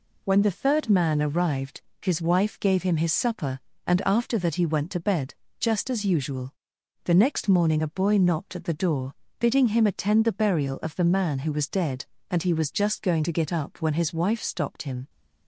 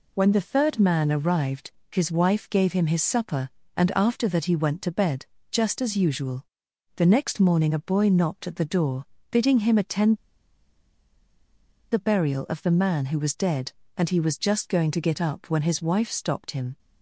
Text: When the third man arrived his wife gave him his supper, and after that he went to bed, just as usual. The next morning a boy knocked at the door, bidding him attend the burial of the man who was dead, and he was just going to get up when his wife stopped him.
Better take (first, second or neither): first